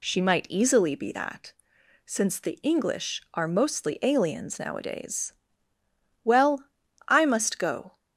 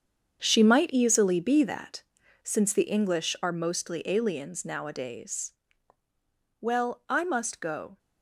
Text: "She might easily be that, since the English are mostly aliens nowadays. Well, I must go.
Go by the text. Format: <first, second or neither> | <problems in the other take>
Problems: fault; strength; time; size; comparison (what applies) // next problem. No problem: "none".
first | gets quieter; strong; throughout; 11.5 dB